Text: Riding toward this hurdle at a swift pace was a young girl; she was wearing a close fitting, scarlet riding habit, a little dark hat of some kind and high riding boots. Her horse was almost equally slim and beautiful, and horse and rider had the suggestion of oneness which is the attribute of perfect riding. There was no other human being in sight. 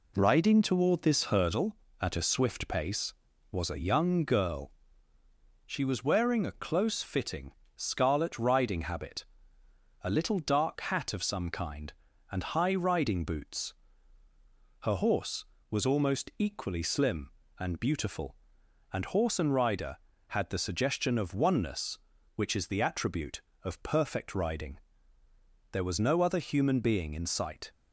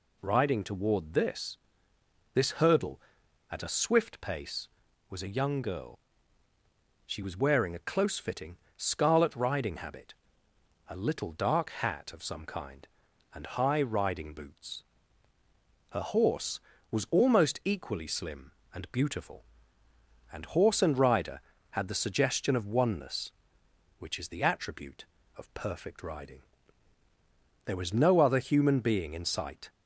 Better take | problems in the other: first | says "this" twice; at 2.3 s

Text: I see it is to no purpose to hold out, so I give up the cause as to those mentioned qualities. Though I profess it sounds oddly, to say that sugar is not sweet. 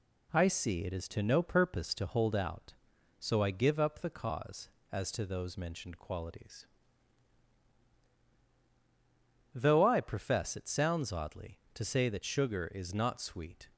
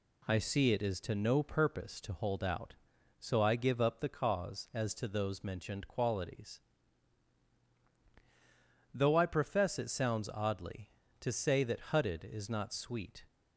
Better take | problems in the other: first | says "hutted" for "sugar"; at 11.9 s

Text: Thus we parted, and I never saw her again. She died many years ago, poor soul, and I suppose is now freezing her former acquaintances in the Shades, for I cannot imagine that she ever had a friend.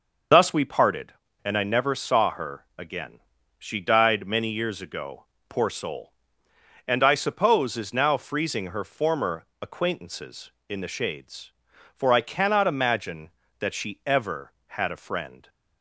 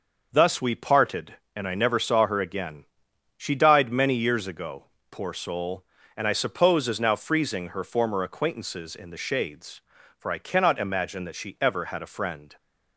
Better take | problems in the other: second | loses the start of "Thus"; at 0.3 s; 90 ms // pauses between "former" and "acquaintances"; slight; at 9.4 s; 0.18 s long

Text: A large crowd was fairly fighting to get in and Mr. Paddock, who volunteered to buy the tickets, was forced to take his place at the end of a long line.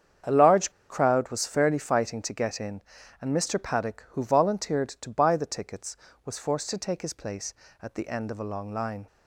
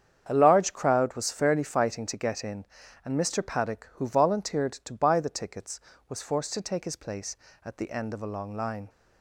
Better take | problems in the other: second | starts louder than the rest; strong; until 1.4 s; 8 dB; strong in the second // pauses between "large" and "crowd"; slight; at 0.7 s; 0.19 s long

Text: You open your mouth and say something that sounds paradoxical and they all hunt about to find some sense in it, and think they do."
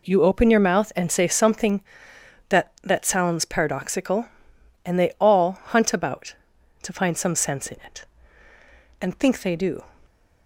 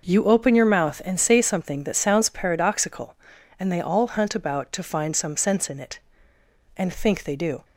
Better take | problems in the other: second | says "that" twice; at 2.8 s

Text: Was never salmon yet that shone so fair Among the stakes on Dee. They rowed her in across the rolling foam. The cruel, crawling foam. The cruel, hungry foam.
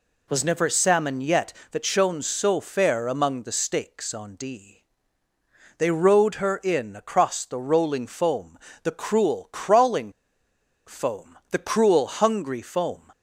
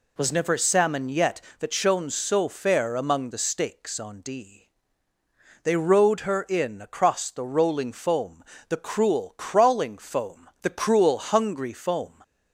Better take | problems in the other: second | pauses between "crawling" and "foam"; noticeable; at 10.1 s; 0.76 s long

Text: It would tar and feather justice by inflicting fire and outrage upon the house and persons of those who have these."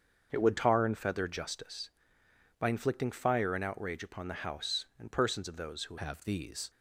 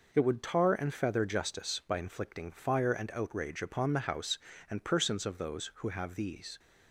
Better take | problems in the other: second | starts louder than the rest; until 1.3 s; 7 dB // changes voice at "have"; from 5.9 s on; 0.7 s long

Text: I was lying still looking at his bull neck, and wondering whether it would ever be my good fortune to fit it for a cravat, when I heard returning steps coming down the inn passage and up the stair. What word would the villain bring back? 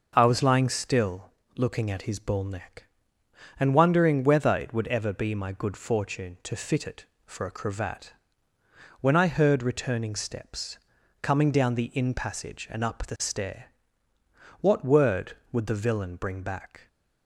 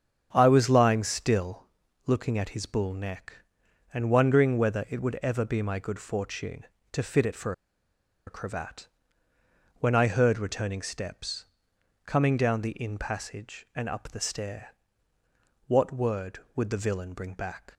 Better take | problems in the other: first | starts louder than the rest; strong; until 1.3 s; 8 dB // pauses between "still" and "looking"; at 1.6 s; 0.42 s long; slight in the first // pauses between "for" and "a"; noticeable; at 7.5 s; 0.73 s long // pauses between "steps" and "coming"; noticeable; at 11.4 s; 0.62 s long; also in the first

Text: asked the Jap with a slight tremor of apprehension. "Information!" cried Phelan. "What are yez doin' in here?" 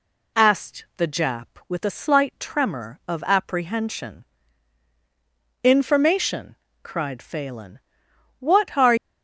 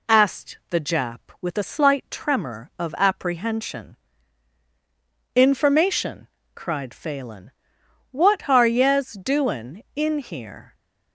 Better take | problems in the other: second | stops before "yez doin in here"; at 8.9 s

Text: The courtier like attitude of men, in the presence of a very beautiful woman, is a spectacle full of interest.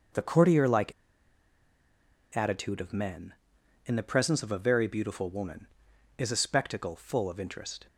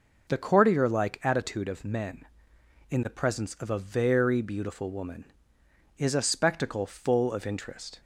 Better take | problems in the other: second | starts louder than the rest; until 2.5 s; 6.5 dB // pauses between "like" and "attitude"; strong; at 0.9 s; 1.4 s long

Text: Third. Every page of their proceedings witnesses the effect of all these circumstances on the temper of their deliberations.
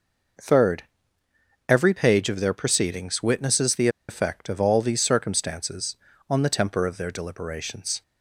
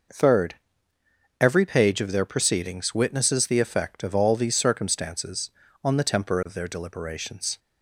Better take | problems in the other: second | pauses between "the" and "effect"; slight; at 3.8 s; 0.20 s long

